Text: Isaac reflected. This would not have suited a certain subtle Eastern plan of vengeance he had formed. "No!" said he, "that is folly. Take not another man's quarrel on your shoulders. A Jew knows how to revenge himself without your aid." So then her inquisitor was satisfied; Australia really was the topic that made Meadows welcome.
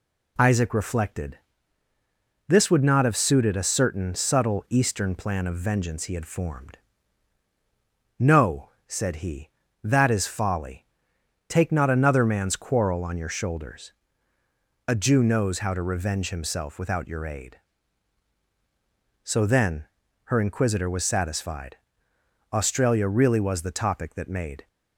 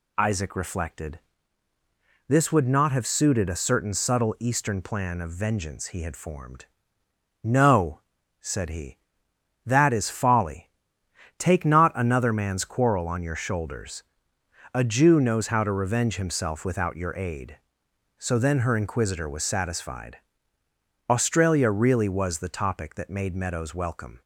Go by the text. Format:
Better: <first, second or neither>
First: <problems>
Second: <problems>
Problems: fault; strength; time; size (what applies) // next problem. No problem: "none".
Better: second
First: pauses between "then" and "her"; at 19.8 s; 0.40 s long // stops before "Meadows welcome"; at 24.6 s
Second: none